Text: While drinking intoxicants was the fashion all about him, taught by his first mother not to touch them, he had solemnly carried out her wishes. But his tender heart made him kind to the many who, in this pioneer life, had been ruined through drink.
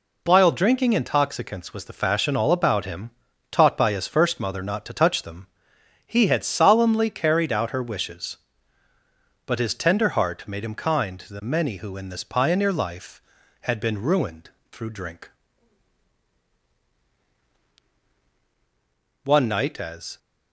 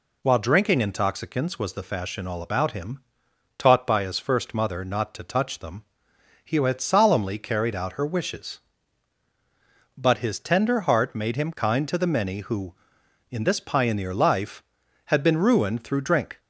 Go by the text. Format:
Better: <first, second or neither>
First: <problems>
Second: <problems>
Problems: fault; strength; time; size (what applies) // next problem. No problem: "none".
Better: second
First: pauses between "ruined" and "through"; slight; at 14.4 s; 0.24 s long // goes on to say "One night as"; noticeable; from 19.2 s on; 0.94 s long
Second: none